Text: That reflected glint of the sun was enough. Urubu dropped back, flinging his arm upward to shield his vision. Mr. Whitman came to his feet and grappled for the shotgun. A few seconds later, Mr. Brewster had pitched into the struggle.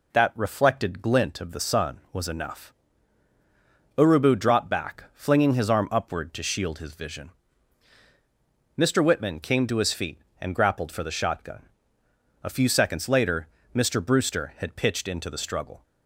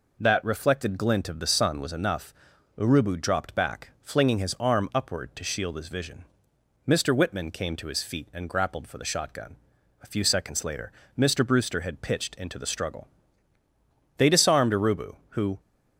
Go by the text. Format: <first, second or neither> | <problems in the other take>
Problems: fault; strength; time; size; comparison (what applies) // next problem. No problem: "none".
first | goes on to say "They disarmed Urubu who"; from 14.1 s on; 1.4 s long